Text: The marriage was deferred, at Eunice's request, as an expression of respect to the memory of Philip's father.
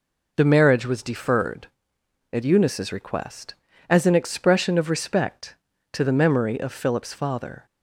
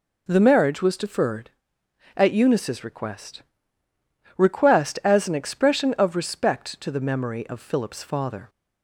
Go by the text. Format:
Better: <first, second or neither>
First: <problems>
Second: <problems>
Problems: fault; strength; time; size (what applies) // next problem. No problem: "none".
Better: first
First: none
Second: says "request" twice; at 4.3 s